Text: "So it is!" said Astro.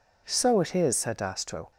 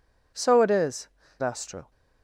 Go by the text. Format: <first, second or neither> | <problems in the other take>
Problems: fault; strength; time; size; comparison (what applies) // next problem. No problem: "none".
first | skips "said"; at 1.2 s